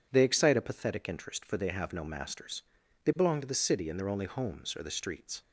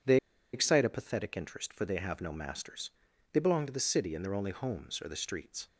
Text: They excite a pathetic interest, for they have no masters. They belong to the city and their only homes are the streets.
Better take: first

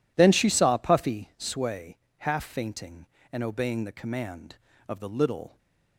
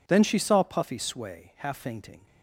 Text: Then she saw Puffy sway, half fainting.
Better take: second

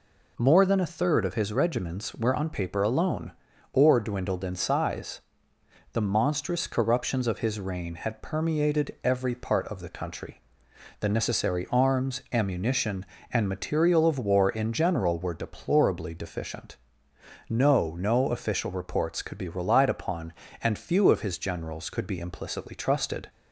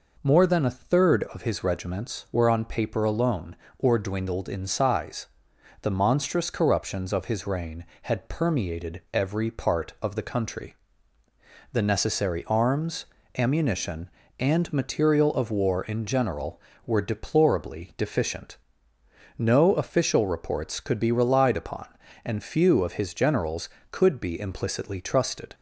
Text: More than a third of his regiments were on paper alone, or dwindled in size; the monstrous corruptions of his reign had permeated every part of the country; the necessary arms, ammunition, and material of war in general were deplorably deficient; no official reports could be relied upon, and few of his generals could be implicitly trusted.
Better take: second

